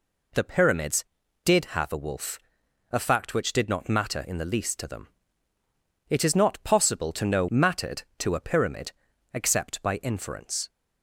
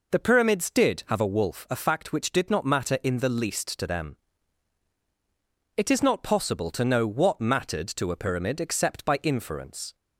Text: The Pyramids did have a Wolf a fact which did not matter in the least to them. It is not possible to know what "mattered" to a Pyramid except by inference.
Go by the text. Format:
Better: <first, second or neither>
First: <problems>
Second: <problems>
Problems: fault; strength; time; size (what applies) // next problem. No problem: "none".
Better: second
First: pauses between "Wolf" and "a"; noticeable; at 2.3 s; 0.54 s long // skips "what"; at 7.4 s // pauses between "Pyramid" and "except"; at 8.9 s; 0.42 s long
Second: none